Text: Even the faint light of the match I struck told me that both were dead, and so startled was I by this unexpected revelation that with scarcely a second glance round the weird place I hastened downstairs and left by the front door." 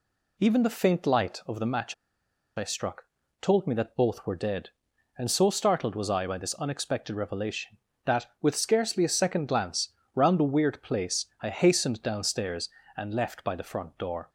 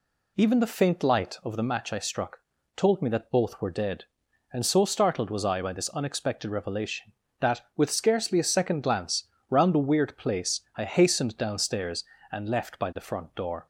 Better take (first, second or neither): second